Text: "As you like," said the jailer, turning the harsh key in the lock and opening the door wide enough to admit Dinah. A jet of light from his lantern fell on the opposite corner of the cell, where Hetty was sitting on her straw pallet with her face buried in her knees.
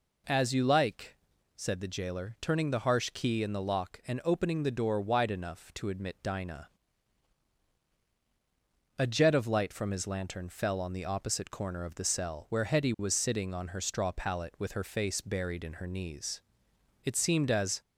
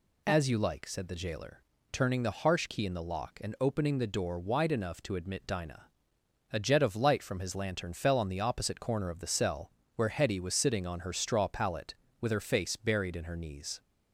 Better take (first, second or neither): second